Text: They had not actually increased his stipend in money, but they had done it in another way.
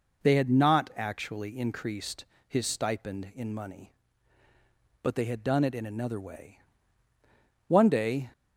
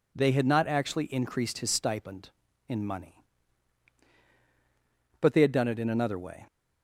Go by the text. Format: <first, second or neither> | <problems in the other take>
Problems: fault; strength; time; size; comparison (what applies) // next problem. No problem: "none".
second | pauses between "increased" and "his"; slight; at 2.2 s; 0.24 s long // goes on to say "One day"; noticeable; from 7.6 s on; 0.64 s long